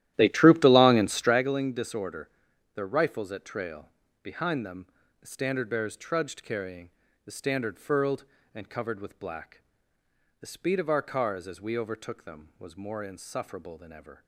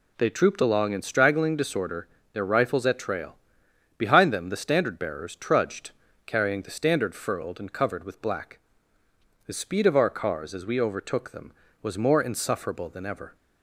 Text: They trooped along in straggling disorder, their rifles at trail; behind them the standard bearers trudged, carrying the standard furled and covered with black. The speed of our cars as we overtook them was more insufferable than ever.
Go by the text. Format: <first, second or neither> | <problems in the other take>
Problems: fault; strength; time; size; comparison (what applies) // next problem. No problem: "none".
second | starts louder than the rest; strong; until 1.5 s; 13 dB // pauses between "them" and "the"; slight; at 4.8 s; 0.36 s long // pauses between "carrying" and "the"; slight; at 6.8 s; 0.34 s long